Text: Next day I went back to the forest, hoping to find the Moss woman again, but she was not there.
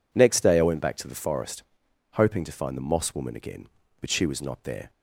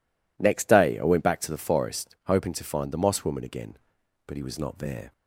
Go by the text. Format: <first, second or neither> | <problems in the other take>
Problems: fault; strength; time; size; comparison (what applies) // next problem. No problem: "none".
first | says "he" for "she"; at 4.3 s